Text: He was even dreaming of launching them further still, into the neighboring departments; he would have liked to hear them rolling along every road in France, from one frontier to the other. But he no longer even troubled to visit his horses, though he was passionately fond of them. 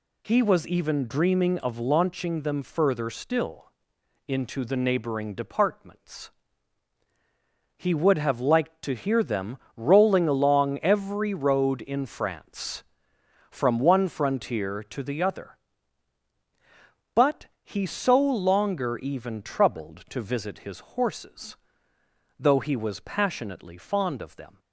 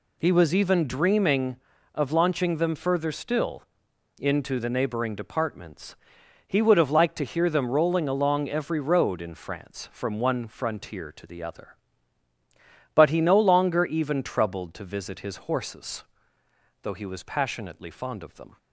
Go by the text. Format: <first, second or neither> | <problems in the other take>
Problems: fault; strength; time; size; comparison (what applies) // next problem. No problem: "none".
second | pauses between "them" and "rolling"; slight; at 9.5 s; 0.18 s long // pauses between "But" and "he"; slight; at 17.4 s; 0.16 s long // says "so" for "no"; at 17.8 s